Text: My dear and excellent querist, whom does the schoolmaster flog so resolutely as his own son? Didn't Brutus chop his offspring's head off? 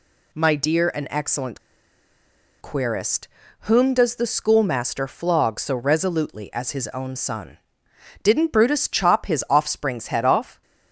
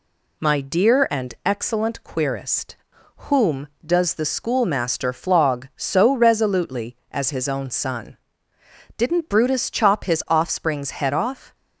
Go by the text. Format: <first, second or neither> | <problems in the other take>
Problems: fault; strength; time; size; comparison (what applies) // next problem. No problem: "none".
second | pauses between "excellent" and "querist"; at 1.6 s; 1.0 s long